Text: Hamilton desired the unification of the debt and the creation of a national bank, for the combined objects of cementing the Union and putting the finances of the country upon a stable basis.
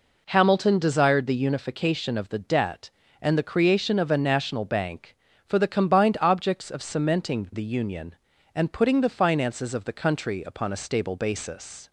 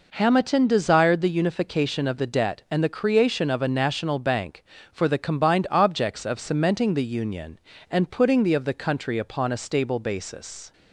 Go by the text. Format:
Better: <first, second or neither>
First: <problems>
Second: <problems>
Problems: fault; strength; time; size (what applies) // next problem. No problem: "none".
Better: first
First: none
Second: skips "finances"; at 8.5 s